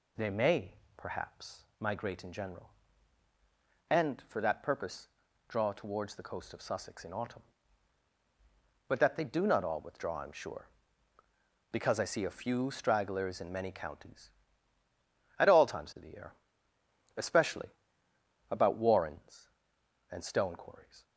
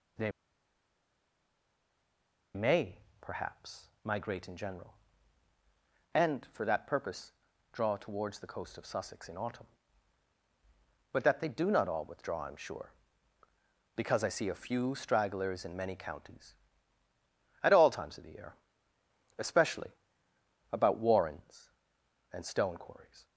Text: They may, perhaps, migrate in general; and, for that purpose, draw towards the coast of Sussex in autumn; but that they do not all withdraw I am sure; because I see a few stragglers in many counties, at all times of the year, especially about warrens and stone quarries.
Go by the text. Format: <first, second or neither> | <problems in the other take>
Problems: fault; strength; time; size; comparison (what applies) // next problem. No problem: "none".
first | pauses between "They" and "may"; strong; at 0.3 s; 2.2 s long // pauses between "especially" and "about"; noticeable; at 19.8 s; 0.82 s long; noticeable in the first